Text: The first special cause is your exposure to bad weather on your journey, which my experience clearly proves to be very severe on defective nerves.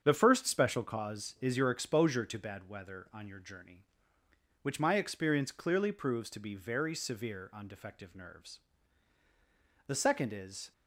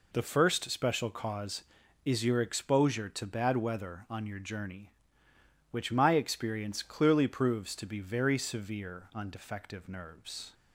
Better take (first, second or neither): second